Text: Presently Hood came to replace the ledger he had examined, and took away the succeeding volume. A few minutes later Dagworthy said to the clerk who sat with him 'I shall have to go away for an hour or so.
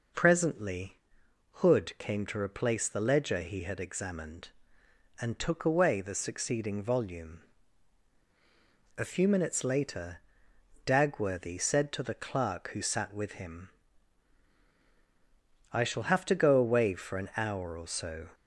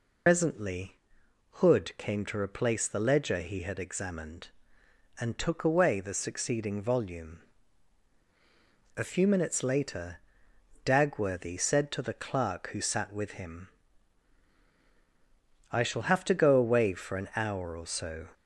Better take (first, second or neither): first